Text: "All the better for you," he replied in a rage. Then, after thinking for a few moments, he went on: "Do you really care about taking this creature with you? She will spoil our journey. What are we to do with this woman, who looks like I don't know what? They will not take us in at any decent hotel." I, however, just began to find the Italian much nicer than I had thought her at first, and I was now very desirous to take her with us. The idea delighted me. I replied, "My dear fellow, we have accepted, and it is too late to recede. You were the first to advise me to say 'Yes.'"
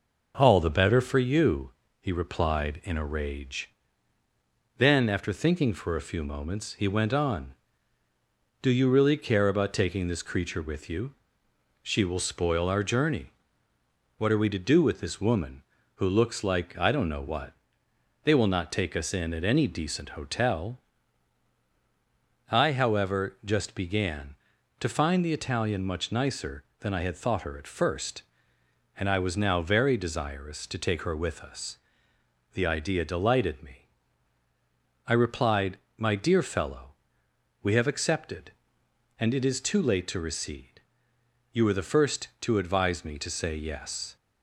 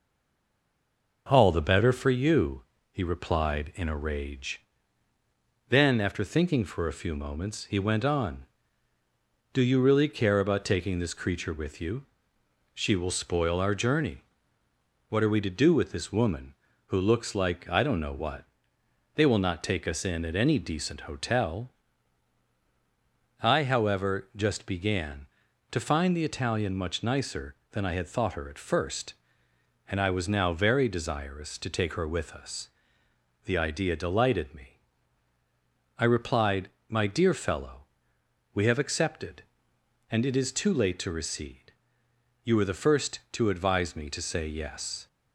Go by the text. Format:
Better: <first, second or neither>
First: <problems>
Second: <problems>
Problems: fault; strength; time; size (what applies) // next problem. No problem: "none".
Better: first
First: none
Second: stays silent before the first word; noticeable; until 1.2 s; 1.2 s long